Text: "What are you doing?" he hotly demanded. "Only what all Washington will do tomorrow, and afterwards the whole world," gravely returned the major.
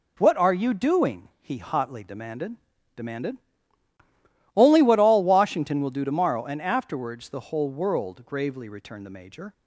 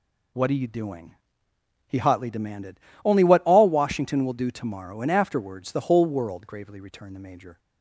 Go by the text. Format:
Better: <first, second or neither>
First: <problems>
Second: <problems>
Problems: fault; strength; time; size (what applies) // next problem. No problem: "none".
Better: second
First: says "demanded" twice; at 2.9 s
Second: none